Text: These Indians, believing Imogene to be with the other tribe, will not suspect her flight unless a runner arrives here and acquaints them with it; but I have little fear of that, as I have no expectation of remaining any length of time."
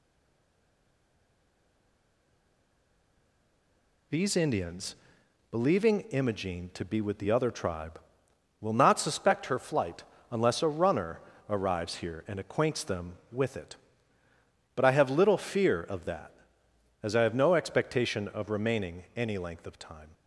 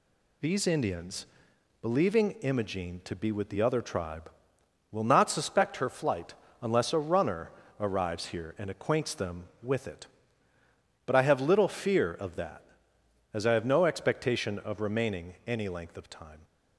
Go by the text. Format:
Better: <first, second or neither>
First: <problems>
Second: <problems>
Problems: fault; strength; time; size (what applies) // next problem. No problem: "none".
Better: second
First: stays silent before the first word; strong; until 4.1 s; 4.1 s long // pauses between "flight" and "unless"; slight; at 10.0 s; 0.28 s long // pauses between "runner" and "arrives"; slight; at 11.2 s; 0.28 s long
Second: pauses between "flight" and "unless"; slight; at 6.3 s; 0.28 s long // pauses between "runner" and "arrives"; slight; at 7.5 s; 0.28 s long